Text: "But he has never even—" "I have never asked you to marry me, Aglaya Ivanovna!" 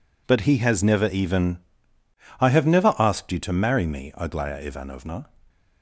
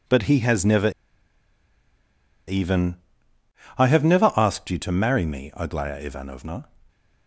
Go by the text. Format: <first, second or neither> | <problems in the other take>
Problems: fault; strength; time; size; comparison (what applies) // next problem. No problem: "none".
first | pauses between "never" and "even"; strong; at 0.8 s; 1.5 s long